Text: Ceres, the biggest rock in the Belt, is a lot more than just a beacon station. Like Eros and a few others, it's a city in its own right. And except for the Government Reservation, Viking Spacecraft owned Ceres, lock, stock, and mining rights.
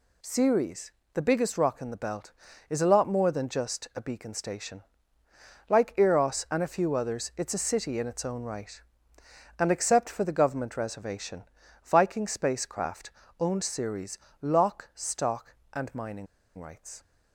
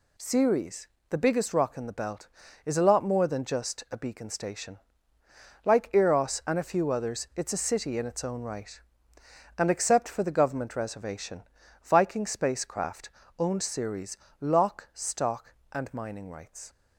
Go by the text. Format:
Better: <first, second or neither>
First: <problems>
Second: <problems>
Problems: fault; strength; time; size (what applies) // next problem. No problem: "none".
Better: second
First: pauses between "Spacecraft" and "owned"; slight; at 13.0 s; 0.30 s long // pauses between "mining" and "rights"; slight; at 16.2 s; 0.31 s long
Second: pauses between "Spacecraft" and "owned"; slight; at 13.0 s; 0.30 s long